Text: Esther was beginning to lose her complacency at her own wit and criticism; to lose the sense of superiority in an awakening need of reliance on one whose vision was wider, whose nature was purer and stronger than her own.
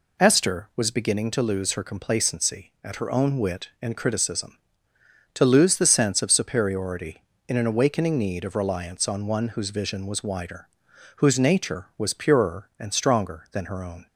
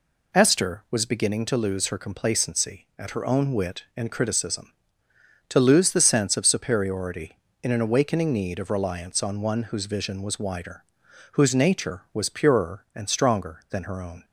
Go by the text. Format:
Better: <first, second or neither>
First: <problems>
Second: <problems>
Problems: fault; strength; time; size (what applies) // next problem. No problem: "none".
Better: neither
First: none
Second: none